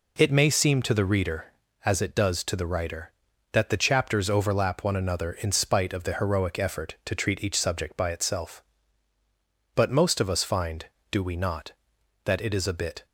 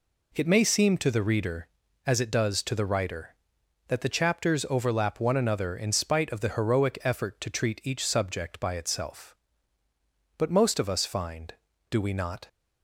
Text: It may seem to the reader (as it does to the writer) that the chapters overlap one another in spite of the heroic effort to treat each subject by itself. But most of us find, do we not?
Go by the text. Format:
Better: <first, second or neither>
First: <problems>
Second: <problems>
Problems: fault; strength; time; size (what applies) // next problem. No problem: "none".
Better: second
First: goes on to say "that it is a bit"; noticeable; from 12.2 s on; 0.80 s long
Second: none